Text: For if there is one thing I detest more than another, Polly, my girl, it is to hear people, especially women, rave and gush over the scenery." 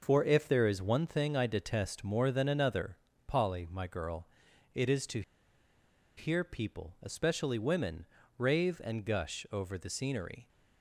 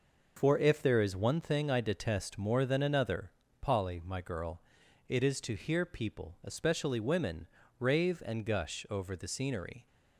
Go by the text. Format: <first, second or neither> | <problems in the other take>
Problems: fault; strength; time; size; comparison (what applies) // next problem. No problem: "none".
second | pauses between "to" and "hear"; noticeable; at 5.2 s; 0.95 s long